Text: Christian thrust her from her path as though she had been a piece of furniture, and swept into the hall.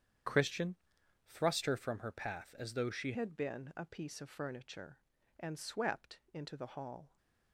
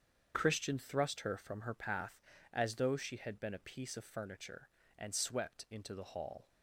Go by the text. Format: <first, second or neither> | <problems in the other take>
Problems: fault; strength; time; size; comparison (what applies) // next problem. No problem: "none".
second | starts louder than the rest; strong; until 1.7 s; 8.5 dB; strong in the second // pauses between "Christian" and "thrust"; noticeable; at 0.7 s; 0.50 s long // changes voice at "had"; from 3.1 s on; 4.0 s long